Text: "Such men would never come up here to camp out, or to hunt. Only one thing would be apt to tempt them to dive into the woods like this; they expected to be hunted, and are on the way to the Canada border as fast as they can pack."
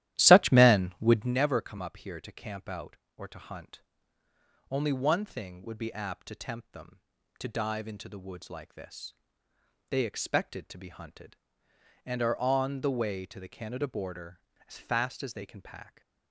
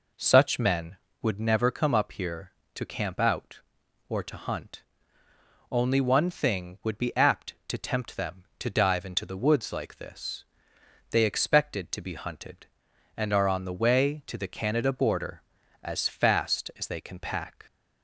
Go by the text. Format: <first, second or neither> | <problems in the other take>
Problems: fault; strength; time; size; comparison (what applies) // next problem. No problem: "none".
second | starts louder than the rest; strong; until 1.3 s; 13 dB